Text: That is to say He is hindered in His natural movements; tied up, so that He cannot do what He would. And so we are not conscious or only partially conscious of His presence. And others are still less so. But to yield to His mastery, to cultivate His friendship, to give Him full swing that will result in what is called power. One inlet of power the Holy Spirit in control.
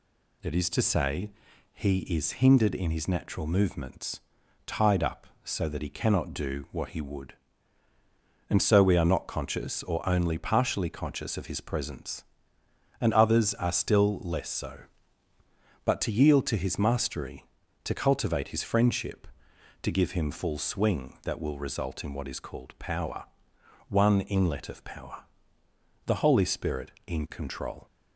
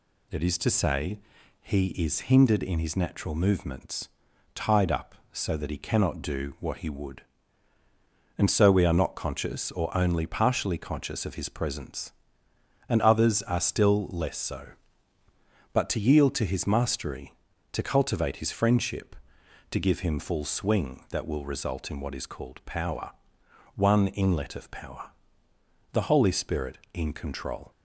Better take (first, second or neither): neither